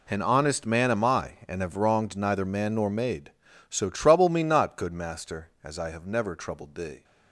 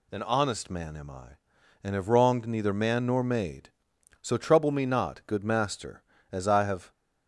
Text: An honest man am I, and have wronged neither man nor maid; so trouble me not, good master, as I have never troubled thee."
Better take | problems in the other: first | stops before "never troubled thee"; at 6.9 s

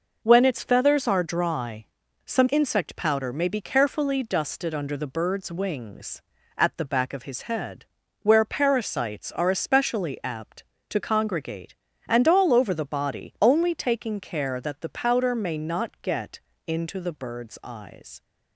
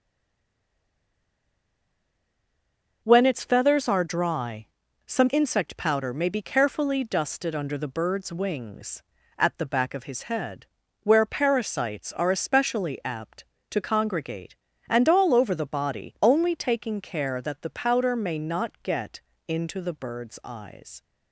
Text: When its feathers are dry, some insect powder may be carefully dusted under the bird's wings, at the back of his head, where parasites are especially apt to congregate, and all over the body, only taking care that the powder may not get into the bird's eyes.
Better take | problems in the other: first | stays silent before the first word; strong; until 3.0 s; 3.0 s long // pauses between "get" and "into"; slight; at 19.1 s; 0.30 s long; slight in the first

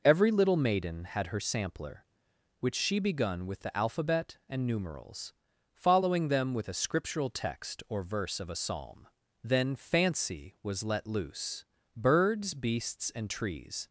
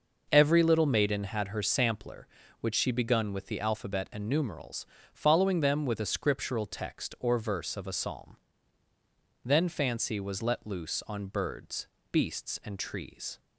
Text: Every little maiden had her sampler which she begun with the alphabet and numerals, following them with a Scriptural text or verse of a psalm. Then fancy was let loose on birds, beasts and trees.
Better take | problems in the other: second | skips "on"; at 11.8 s

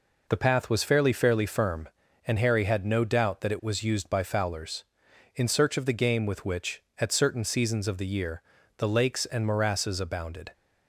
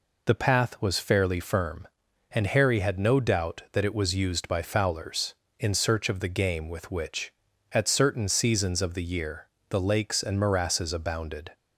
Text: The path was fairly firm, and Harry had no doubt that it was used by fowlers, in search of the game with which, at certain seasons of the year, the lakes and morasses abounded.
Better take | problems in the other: second | says "fairly" twice; at 1.1 s

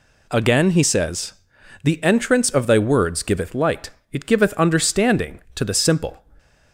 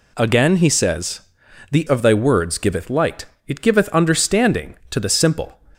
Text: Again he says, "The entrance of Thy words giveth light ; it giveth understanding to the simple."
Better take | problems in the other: first | skips "entrance"; at 1.8 s

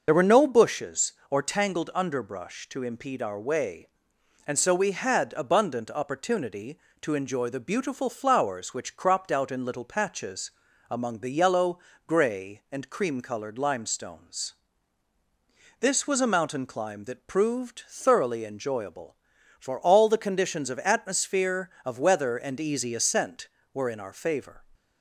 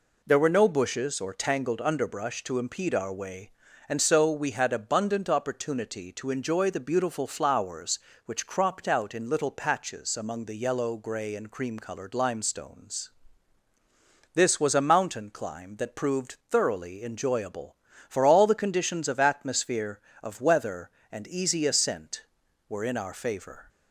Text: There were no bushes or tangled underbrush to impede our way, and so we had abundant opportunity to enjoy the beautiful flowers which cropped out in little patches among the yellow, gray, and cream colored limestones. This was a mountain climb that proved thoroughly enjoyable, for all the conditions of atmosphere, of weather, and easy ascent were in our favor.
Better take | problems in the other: second | loses the start of "There"; at 0.0 s; 35 ms // pauses between "patches" and "among"; at 10.5 s; 0.40 s long

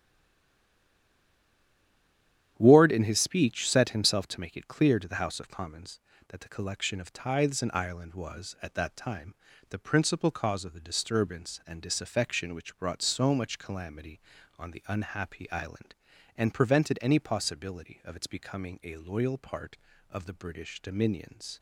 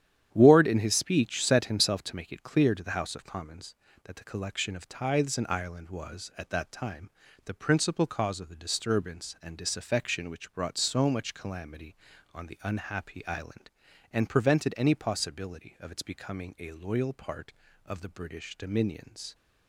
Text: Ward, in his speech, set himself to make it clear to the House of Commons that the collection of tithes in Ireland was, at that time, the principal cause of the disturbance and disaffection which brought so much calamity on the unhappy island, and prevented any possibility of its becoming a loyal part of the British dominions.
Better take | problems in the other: second | stays silent before the first word; strong; until 2.5 s; 2.5 s long // starts louder than the rest; strong; until 3.5 s; 10 dB; strong in the second

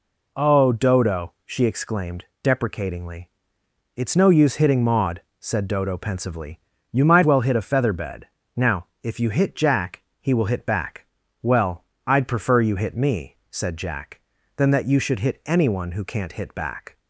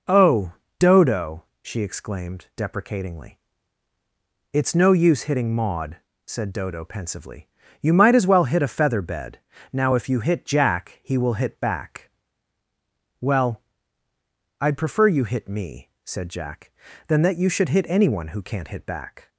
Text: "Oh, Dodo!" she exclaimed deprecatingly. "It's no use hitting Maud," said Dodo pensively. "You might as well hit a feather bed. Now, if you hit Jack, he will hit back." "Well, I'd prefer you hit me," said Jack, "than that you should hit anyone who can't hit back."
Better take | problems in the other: second | pauses between "exclaimed" and "deprecatingly"; slight; at 2.2 s; 0.16 s long // skips "as"; at 7.2 s

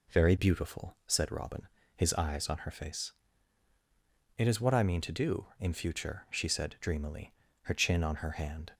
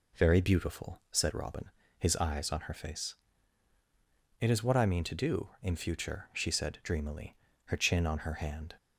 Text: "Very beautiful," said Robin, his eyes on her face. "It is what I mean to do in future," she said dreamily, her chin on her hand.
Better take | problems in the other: neither | none

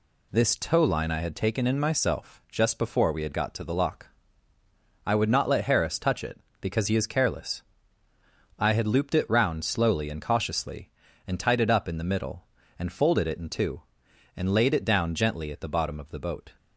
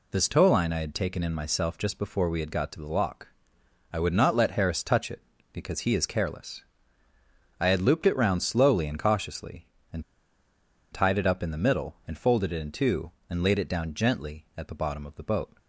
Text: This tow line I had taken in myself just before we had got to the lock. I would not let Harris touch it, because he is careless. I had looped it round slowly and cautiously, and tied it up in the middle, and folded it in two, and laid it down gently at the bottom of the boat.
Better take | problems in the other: first | pauses between "and" and "tied"; noticeable; at 10.0 s; 0.89 s long

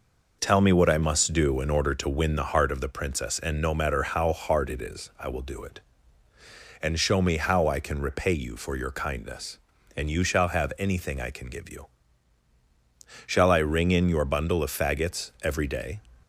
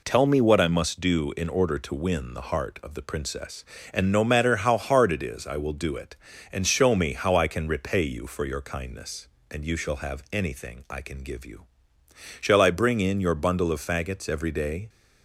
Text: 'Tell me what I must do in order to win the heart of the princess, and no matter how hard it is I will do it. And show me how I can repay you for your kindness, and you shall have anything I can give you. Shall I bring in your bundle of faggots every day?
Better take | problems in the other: second | says "ring" for "bring"; at 13.5 s

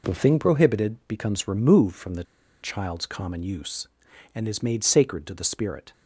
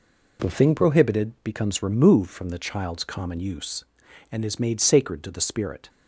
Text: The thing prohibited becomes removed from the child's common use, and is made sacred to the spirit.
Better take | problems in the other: second | pauses between "the" and "child's"; at 2.2 s; 0.39 s long

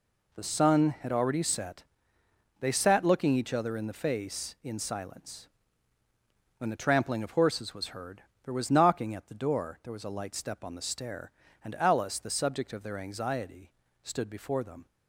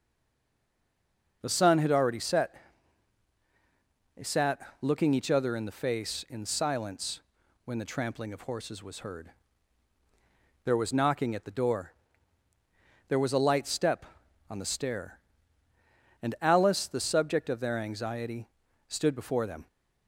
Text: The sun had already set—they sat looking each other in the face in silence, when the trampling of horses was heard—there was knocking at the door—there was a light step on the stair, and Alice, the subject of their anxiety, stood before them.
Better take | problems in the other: first | stays silent before the first word; noticeable; until 1.4 s; 1.4 s long // pauses between "sat" and "looking"; slight; at 4.5 s; 0.22 s long

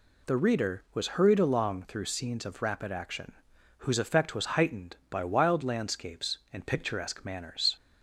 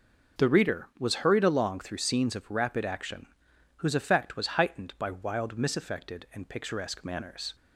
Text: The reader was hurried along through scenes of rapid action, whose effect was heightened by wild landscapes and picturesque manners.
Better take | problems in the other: first | says "misaffected" for "landscapes"; at 5.5 s

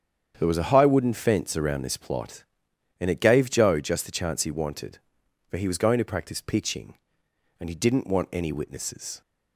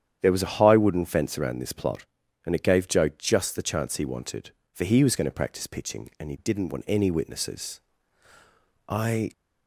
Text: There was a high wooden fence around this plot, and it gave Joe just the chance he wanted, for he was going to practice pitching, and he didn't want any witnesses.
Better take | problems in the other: first | starts louder than the rest; strong; until 1.2 s; 9.5 dB; strong in the first // goes on to say "I"; slight; from 8.8 s on; 0.44 s long

